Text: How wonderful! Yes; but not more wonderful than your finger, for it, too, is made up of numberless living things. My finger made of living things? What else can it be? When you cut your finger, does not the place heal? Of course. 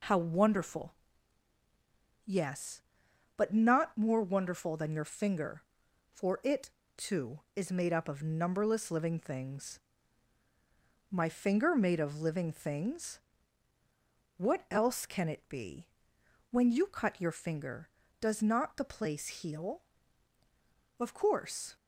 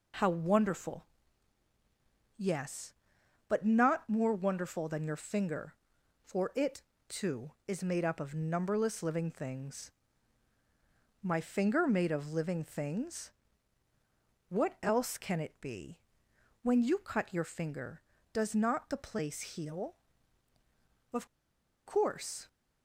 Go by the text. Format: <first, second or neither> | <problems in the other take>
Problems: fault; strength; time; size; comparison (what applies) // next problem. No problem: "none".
first | pauses between "Of" and "course"; noticeable; at 21.2 s; 0.59 s long